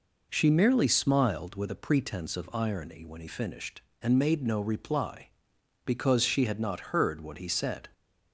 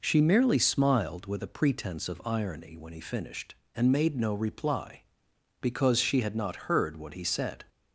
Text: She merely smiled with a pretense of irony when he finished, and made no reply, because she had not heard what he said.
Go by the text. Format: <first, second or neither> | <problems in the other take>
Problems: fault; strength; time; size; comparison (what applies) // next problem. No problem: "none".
neither | none